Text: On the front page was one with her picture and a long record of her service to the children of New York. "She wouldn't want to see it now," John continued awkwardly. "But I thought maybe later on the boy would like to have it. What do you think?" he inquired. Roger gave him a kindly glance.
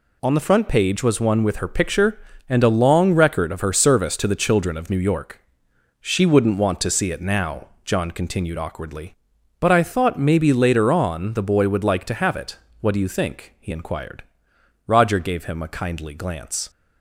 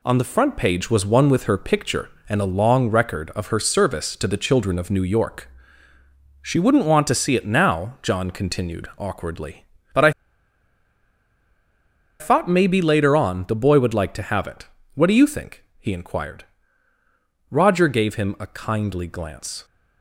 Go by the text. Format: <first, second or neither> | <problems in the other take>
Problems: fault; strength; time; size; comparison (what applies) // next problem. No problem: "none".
first | pauses between "I" and "thought"; strong; at 10.0 s; 2.0 s long